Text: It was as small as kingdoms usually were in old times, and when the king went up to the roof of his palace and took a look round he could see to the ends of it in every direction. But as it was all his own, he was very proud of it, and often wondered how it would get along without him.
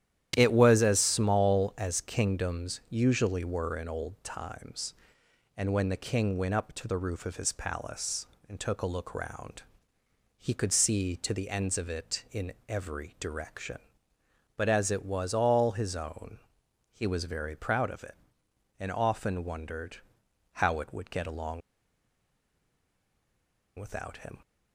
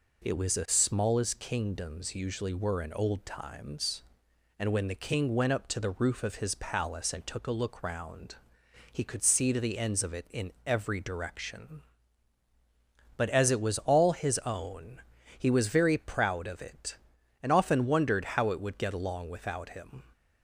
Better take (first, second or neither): second